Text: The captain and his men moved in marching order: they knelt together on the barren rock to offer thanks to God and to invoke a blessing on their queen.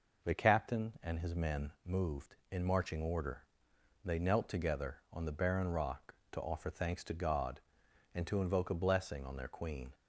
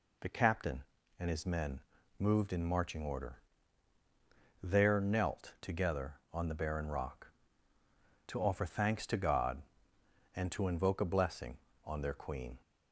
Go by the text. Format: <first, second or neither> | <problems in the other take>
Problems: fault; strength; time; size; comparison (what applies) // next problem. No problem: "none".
first | pauses between "men" and "moved"; at 1.8 s; 0.38 s long // says "there" for "they"; at 4.6 s